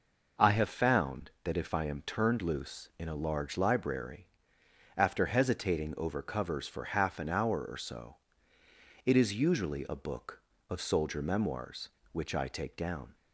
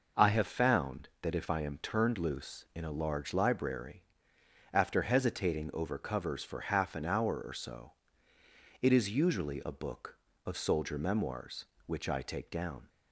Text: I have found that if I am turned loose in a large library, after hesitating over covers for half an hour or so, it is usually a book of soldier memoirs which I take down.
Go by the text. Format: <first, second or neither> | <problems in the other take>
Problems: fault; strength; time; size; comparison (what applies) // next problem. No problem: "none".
neither | none